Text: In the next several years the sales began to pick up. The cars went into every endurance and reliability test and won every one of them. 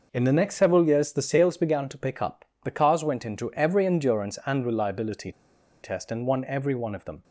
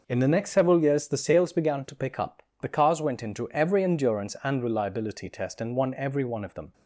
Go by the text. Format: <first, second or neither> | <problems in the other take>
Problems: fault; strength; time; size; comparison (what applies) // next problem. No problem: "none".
second | pauses between "reliability" and "test"; noticeable; at 5.3 s; 0.50 s long